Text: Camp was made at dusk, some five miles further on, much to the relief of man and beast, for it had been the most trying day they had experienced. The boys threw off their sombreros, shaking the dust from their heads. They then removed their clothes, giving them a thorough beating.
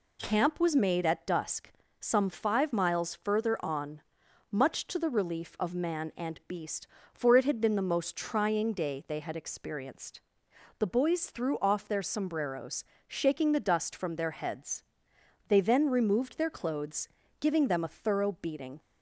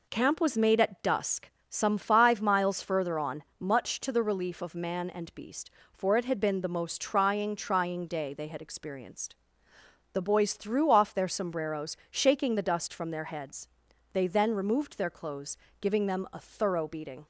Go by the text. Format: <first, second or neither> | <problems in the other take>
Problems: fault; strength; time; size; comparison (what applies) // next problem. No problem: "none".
first | says "trying" twice; at 7.5 s